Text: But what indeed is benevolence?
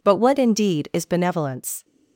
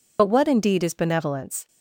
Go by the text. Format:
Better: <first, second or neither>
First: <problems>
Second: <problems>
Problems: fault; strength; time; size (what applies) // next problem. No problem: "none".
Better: first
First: none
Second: loses the start of "But"; at 0.1 s; 45 ms